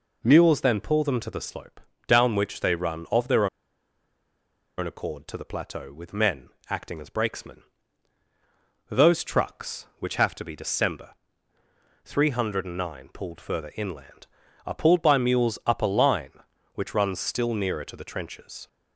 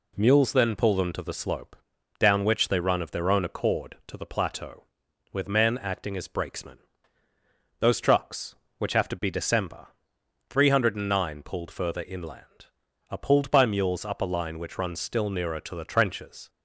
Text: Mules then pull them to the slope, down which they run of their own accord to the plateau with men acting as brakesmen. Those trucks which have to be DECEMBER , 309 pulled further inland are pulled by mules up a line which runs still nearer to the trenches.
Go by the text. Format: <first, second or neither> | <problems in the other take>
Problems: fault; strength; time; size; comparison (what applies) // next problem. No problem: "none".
second | pauses between "their" and "own"; strong; at 3.4 s; 1.3 s long // pauses between "men" and "acting"; slight; at 6.4 s; 0.20 s long